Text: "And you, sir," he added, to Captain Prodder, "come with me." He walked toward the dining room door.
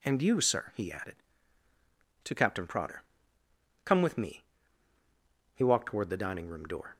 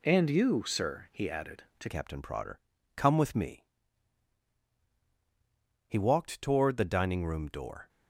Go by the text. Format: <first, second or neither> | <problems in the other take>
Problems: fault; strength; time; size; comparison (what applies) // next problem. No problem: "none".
first | changes voice at "Captain"; from 1.8 s on; 6.0 s long